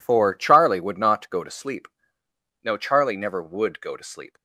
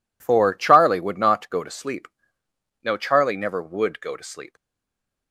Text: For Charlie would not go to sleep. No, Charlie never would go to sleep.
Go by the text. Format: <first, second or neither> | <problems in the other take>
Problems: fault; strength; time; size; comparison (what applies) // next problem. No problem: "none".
first | stays silent after the last word; slight; from 4.5 s on; 0.8 s long